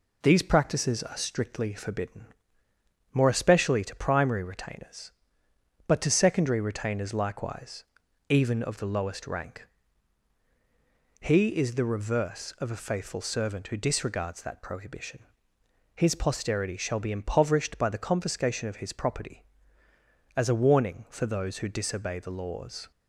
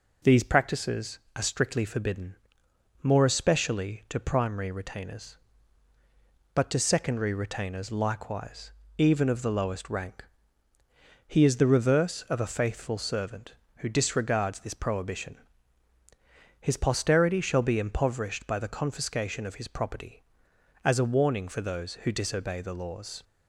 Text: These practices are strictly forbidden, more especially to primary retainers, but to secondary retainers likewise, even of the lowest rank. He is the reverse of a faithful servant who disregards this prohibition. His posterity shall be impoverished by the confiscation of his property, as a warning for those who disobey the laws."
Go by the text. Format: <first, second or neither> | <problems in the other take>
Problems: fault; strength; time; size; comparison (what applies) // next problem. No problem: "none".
second | says "that" for "this"; at 14.4 s